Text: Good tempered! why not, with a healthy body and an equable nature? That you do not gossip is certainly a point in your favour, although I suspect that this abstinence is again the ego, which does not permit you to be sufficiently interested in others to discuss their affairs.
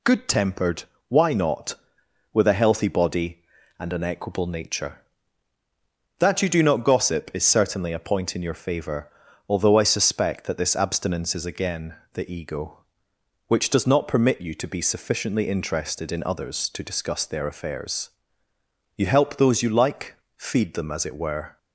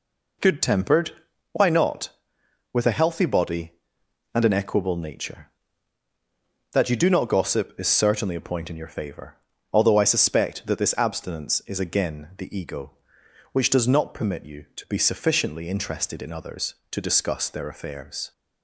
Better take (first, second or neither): second